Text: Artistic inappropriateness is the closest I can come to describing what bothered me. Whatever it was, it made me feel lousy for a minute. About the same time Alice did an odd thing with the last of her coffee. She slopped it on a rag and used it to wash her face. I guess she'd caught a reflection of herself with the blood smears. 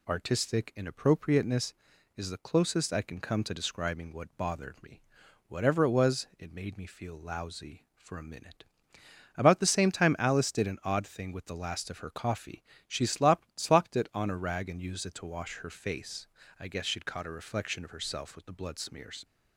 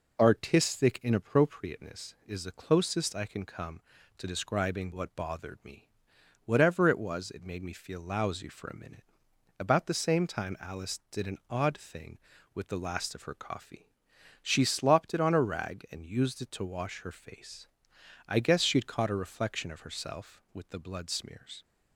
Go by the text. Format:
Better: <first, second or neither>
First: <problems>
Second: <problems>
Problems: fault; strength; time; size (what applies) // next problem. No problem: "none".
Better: second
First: says "slopped" twice; at 13.5 s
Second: none